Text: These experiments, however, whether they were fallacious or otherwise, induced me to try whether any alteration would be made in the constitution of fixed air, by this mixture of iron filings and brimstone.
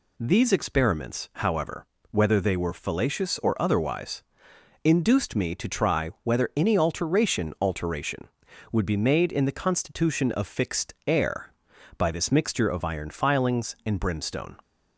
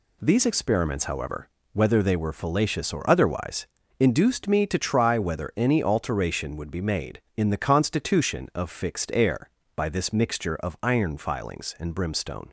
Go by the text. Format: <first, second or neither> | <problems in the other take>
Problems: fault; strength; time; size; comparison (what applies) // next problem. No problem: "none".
second | says "alteration" twice; at 7.6 s